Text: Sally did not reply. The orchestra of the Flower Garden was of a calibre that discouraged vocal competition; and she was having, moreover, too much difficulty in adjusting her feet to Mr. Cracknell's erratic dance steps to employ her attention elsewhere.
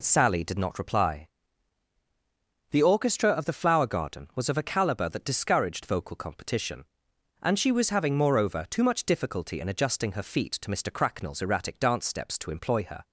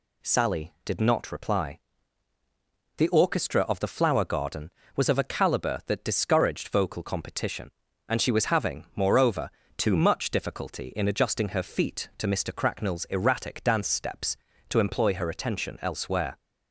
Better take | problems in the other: second | stops before "attention elsewhere"; at 13.0 s

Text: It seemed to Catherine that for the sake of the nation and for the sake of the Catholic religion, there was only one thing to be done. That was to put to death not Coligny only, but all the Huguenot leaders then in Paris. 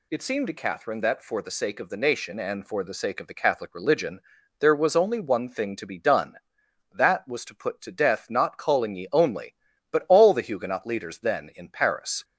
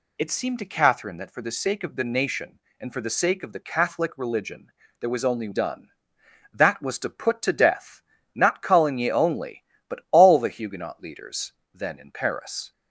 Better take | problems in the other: first | skips "one thing to be"; at 5.5 s // pauses between "death" and "not"; slight; at 8.0 s; 0.36 s long // pauses between "leaders" and "then"; slight; at 11.5 s; 0.20 s long

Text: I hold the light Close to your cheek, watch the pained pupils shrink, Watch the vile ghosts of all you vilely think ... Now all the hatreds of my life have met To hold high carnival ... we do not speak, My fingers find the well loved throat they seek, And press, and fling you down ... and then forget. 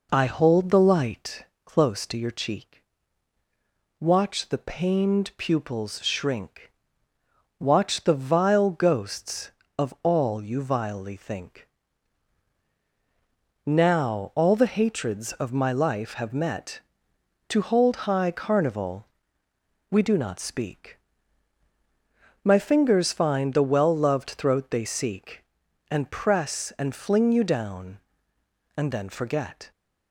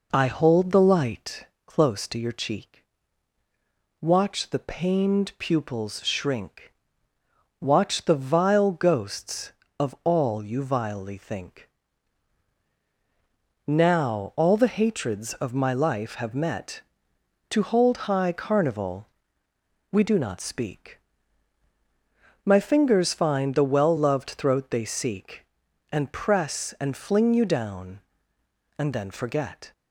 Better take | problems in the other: neither | pauses between "light" and "Close"; slight; the same in both

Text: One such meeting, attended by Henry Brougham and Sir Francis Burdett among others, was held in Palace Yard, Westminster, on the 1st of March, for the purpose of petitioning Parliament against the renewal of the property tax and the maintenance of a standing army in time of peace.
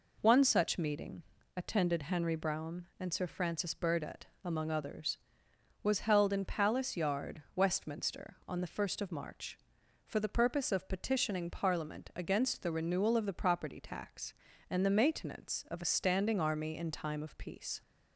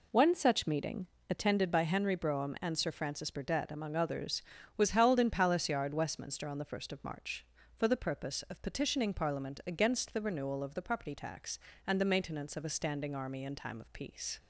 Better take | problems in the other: second | skips "by"; at 2.0 s // pauses between "Burdett" and "among"; slight; at 4.2 s; 0.16 s long

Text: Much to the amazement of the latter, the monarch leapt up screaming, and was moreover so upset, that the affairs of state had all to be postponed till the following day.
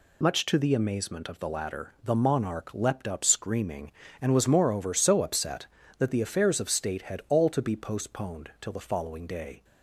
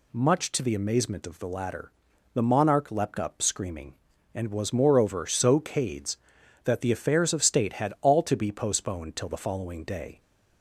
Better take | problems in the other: first | says "cades" for "upset"; at 5.5 s

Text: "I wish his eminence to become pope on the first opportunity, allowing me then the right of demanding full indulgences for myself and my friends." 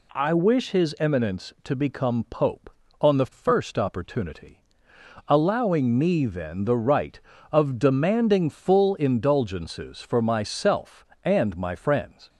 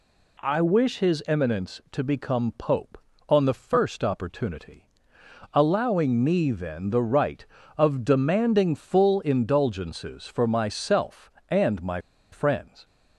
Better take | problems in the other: first | pauses between "my" and "friends"; slight; at 12.0 s; 0.31 s long

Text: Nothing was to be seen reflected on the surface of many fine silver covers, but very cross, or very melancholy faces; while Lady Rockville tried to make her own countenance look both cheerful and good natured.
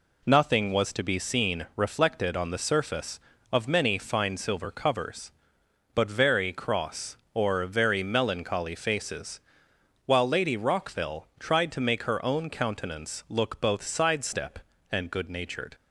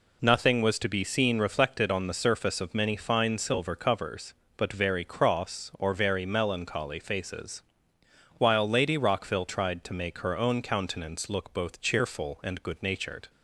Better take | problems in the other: second | says "sidestep" for "cheerful"; at 13.8 s

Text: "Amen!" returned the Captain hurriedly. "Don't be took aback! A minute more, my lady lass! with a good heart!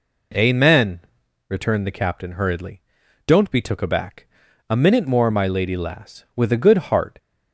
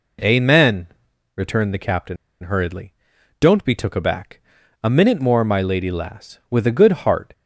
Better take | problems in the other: first | pauses between "Captain" and "hurriedly"; slight; at 2.1 s; 0.26 s long

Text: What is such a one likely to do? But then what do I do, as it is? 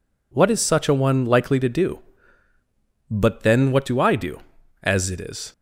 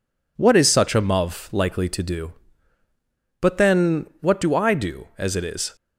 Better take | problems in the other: first | says "muv" for "one"; at 1.0 s

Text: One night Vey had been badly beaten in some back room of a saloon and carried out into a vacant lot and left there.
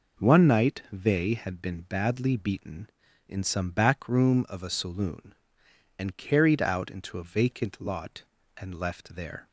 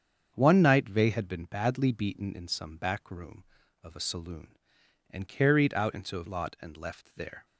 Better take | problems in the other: first | starts louder than the rest; strong; until 1.3 s; 7.5 dB // skips "vacant"; at 6.2 s

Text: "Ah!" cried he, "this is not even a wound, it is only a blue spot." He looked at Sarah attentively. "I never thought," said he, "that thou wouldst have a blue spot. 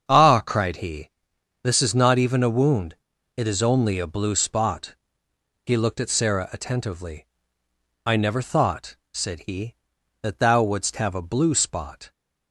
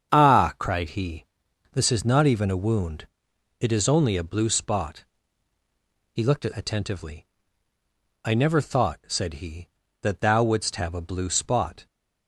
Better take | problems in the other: first | starts louder than the rest; strong; until 1.1 s; 7.5 dB; strong in the first // skips "Sarah"; at 6.5 s

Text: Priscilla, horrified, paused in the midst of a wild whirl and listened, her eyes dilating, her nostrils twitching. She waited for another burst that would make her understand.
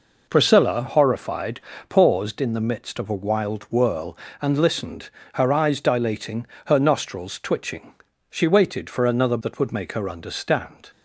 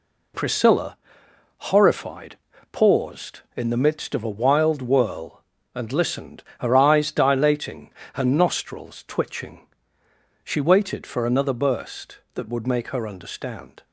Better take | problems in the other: second | skips "burst"; at 9.4 s

